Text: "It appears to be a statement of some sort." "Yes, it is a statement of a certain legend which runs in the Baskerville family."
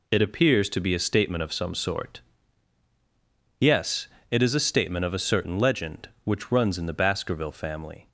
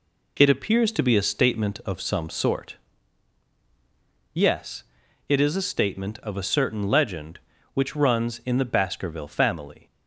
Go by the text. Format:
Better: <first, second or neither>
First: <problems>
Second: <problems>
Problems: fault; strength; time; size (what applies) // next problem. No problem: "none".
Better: neither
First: none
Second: none